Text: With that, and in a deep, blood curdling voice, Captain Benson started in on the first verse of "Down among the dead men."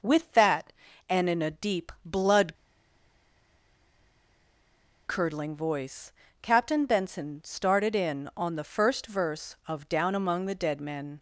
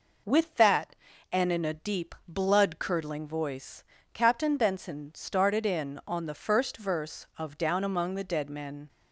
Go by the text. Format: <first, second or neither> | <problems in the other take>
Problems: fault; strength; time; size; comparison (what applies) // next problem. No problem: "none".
second | pauses between "blood" and "curdling"; strong; at 2.5 s; 2.5 s long